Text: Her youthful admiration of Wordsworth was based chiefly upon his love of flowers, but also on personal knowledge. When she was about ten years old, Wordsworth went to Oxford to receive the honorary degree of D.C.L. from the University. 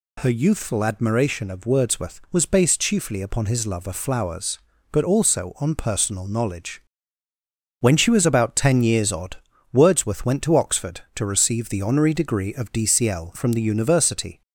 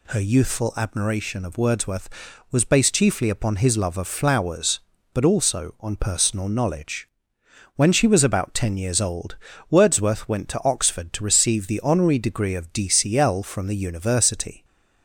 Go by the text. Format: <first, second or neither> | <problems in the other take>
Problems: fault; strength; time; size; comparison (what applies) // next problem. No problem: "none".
second | says "odd" for "old"; at 9.1 s